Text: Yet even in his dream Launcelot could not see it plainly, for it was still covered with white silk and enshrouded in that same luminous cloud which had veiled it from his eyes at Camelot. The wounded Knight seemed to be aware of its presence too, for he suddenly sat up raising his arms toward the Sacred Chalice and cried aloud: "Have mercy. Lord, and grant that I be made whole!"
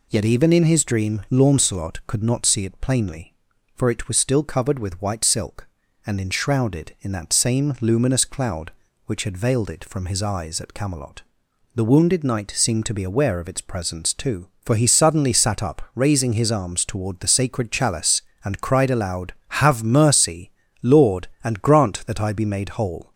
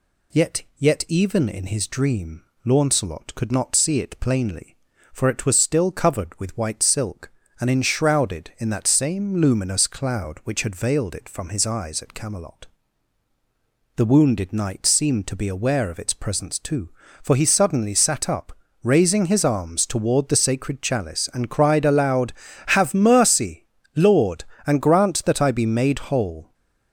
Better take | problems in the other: first | says "Yet" twice; at 0.7 s // pauses between "dream" and "Launcelot"; slight; at 2.4 s; 0.22 s long // pauses between "up" and "raising"; slight; at 18.5 s; 0.32 s long

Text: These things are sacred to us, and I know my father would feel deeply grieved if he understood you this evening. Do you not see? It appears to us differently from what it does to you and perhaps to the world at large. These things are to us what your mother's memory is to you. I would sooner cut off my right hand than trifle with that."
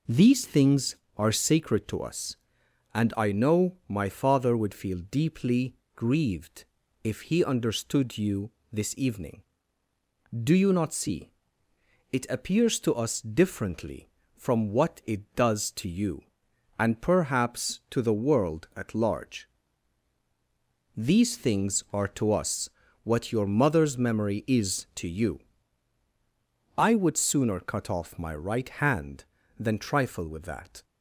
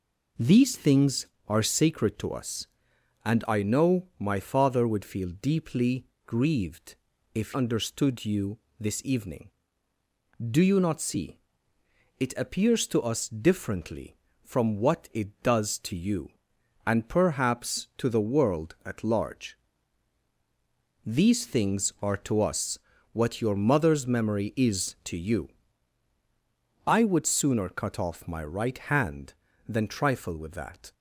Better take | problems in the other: first | pauses between "deeply" and "grieved"; slight; at 6.0 s; 0.22 s long; slight in the first // pauses between "grieved" and "if"; at 6.9 s; 0.40 s long; also in the first // skips "he"; at 7.5 s // pauses between "you" and "this"; slight; at 8.5 s; 0.20 s long; slight in the first // pauses between "us" and "what"; slight; at 22.7 s; 0.36 s long; slight in the first

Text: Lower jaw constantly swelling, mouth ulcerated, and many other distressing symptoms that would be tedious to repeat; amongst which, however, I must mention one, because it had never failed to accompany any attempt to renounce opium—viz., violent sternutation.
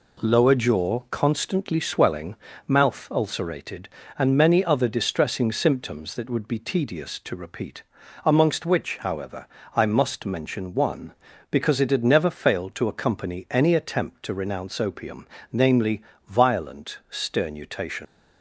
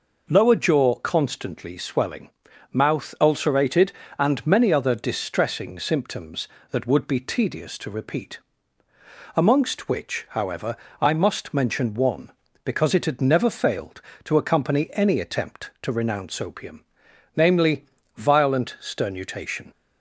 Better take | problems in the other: second | leaves "sternutation" unfinished; at 18.0 s; 150 ms

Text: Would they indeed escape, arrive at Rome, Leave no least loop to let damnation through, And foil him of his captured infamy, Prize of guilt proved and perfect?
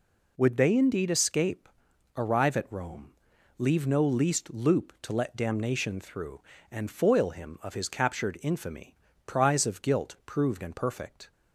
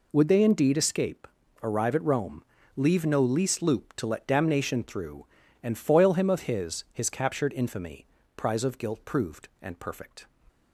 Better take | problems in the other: first | says "his" twice; at 6.9 s

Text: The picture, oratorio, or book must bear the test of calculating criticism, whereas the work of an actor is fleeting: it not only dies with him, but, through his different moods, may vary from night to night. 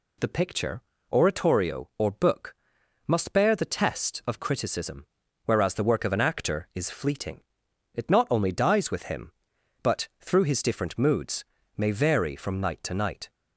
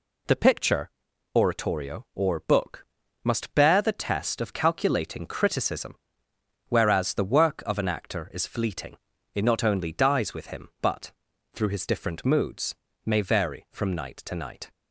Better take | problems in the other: second | pauses between "book" and "must"; noticeable; at 2.5 s; 0.54 s long; also in the second // skips "calculating"; at 4.3 s

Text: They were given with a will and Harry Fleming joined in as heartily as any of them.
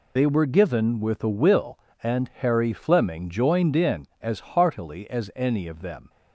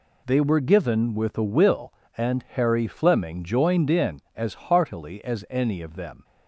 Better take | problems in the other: second | loses the start of "They"; at 0.1 s; 45 ms

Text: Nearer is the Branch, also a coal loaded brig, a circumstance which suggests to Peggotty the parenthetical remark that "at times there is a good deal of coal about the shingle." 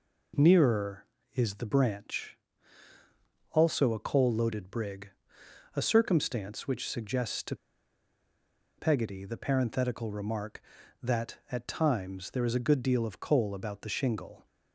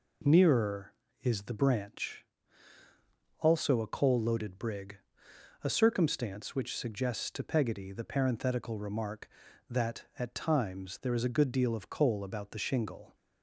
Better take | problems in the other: second | pauses between "to" and "Peggotty"; at 7.5 s; 1.2 s long

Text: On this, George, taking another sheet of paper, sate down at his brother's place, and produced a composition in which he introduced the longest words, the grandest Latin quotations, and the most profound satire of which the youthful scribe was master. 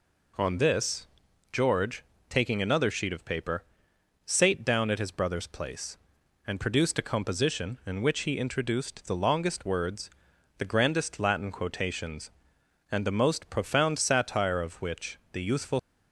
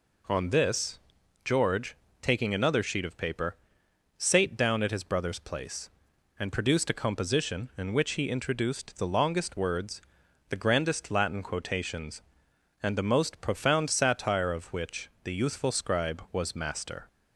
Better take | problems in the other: second | stops before "scribe was master"; at 15.7 s

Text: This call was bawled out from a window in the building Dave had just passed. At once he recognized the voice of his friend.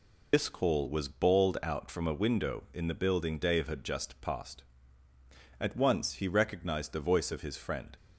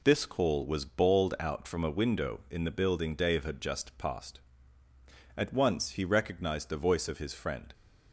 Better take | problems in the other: second | loses the start of "This"; at 0.3 s; 55 ms

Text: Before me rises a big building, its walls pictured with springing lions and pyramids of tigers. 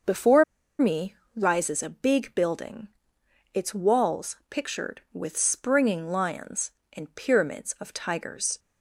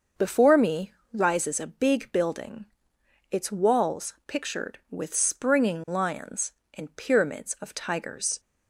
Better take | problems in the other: second | starts louder than the rest; until 1.6 s; 6 dB; also in the second // pauses between "Before" and "me"; slight; at 0.4 s; 0.35 s long // pauses between "me" and "rises"; slight; at 1.1 s; 0.20 s long; slight in the second

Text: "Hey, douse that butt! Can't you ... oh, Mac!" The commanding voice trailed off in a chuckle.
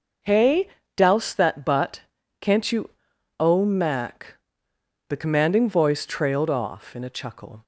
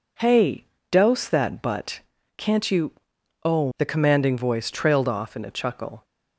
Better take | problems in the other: first | skips "Mac"; at 3.7 s

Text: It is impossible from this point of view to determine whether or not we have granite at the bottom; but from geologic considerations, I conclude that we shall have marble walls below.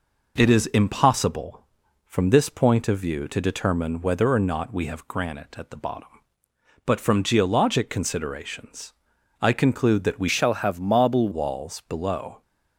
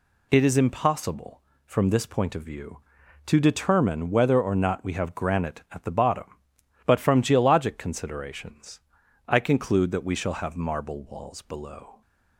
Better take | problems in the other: second | changes voice from "shall" to "marble"; from 10.2 to 11.2 s; 1.0 s long

